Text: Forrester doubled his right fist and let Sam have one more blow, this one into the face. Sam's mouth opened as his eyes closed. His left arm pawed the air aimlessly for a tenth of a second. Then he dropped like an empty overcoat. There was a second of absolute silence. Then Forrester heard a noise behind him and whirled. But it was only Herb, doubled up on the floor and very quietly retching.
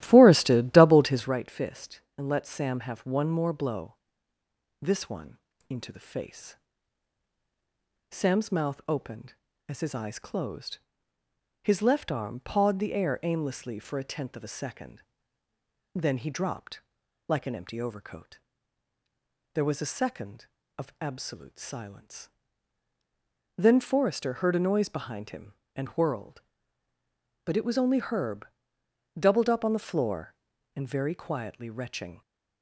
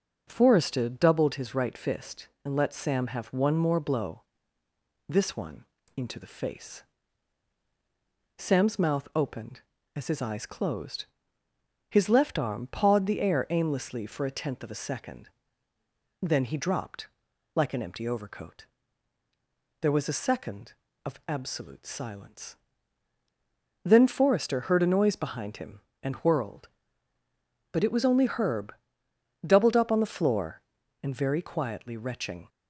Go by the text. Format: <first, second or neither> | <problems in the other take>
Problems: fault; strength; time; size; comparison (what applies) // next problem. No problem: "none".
second | starts louder than the rest; strong; until 1.3 s; 14 dB // pauses between "one" and "into"; slight; at 5.3 s; 0.32 s long; slight in the second // pauses between "dropped" and "like"; noticeable; at 16.8 s; 0.46 s long; noticeable in the second